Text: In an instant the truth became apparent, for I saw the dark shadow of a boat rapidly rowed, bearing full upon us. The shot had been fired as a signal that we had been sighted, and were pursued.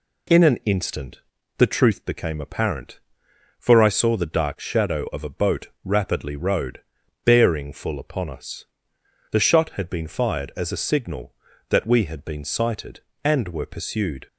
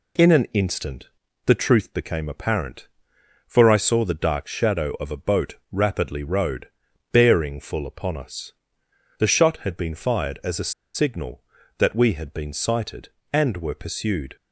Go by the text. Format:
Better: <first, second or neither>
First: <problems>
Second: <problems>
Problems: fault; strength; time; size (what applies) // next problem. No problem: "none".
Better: first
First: pauses between "instant" and "the"; slight; at 1.2 s; 0.36 s long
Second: pauses between "instant" and "the"; slight; at 1.0 s; 0.36 s long // pauses between "a" and "signal"; slight; at 10.7 s; 0.24 s long